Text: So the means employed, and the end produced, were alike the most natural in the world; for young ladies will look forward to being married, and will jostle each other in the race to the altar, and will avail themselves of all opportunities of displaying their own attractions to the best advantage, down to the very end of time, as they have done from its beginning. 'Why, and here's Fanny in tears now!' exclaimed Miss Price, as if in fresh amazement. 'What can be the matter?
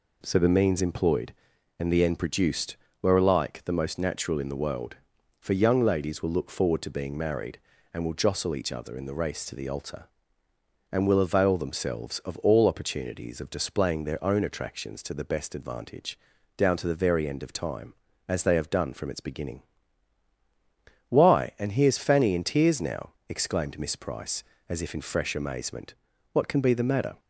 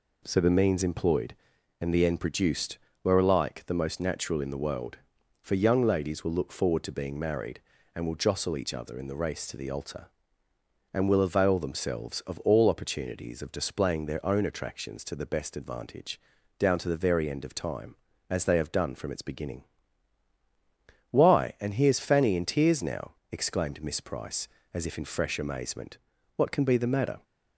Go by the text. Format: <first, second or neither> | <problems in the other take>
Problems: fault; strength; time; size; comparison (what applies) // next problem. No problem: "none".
neither | none